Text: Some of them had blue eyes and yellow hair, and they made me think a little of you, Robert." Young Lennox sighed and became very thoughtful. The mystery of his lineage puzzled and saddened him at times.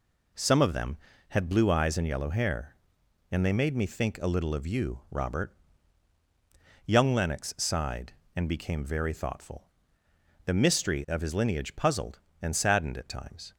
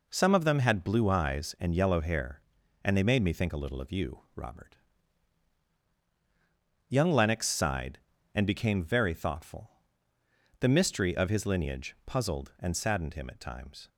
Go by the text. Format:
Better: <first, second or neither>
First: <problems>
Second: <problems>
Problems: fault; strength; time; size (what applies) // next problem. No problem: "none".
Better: second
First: skips "him"; at 12.9 s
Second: none